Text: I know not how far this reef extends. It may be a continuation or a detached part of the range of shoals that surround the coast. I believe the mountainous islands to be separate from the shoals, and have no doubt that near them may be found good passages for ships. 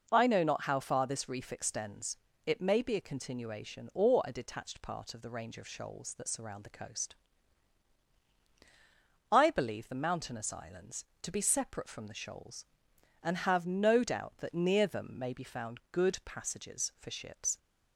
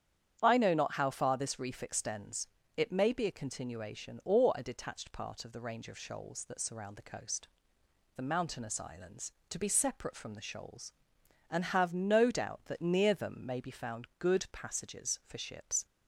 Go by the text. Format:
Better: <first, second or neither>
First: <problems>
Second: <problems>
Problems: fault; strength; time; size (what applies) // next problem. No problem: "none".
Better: first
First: none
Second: starts louder than the rest; strong; until 1.4 s; 9 dB // skips "I believe"; at 7.8 s